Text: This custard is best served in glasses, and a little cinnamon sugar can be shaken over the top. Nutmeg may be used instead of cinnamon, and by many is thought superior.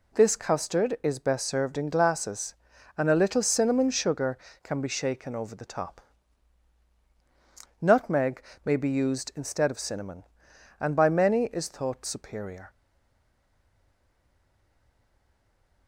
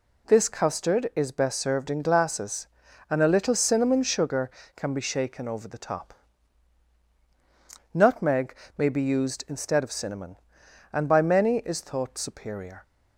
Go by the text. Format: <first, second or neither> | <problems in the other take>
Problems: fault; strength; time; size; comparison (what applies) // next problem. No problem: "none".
second | pauses between "Nutmeg" and "may"; slight; at 8.4 s; 0.24 s long; slight in the second // stays silent after the last word; strong; from 12.6 s on; 3.2 s long